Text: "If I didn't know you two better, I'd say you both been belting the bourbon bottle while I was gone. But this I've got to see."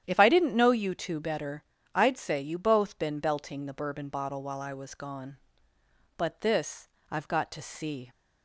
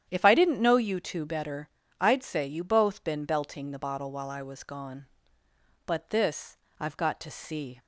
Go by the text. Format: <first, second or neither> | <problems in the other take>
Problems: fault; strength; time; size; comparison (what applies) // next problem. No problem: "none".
first | starts louder than the rest; strong; until 1.1 s; 10 dB; strong in the first // skips "bourbon"; at 3.7 s // pauses between "this" and "I've"; slight; at 6.5 s; 0.24 s long; slight in the first